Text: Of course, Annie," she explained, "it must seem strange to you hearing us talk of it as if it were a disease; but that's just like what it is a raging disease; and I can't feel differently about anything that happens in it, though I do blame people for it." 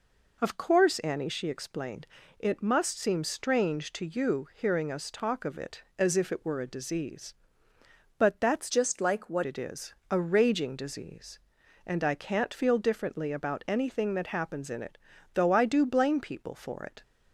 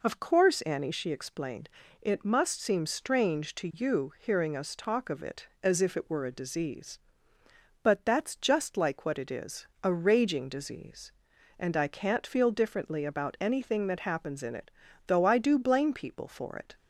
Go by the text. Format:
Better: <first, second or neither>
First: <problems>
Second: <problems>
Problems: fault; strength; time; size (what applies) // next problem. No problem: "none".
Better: second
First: changes voice from "just" to "what"; from 8.6 to 9.4 s; 0.8 s long // pauses between "is" and "a"; slight; at 9.9 s; 0.16 s long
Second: pauses between "is" and "a"; slight; at 9.6 s; 0.16 s long